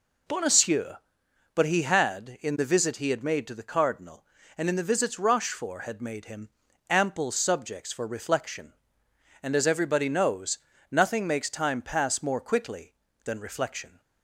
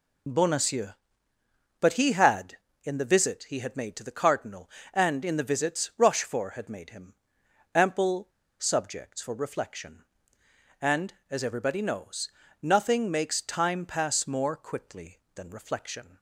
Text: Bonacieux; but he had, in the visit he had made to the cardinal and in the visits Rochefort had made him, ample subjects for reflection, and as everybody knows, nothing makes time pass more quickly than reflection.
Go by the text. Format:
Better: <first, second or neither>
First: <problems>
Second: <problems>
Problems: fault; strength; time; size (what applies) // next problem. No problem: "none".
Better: first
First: none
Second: pauses between "ample" and "subjects"; slight; at 8.2 s; 0.31 s long